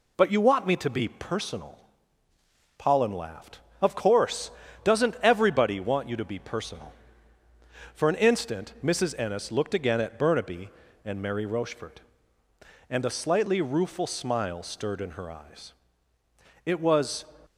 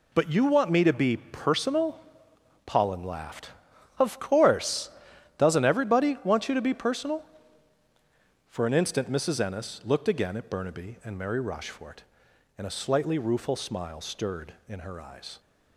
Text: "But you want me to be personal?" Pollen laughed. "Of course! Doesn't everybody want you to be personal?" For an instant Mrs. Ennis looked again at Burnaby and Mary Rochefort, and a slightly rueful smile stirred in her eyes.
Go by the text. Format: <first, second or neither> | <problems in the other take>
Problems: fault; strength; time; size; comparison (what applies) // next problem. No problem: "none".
second | goes on to say "It was"; noticeable; from 16.6 s on; 0.62 s long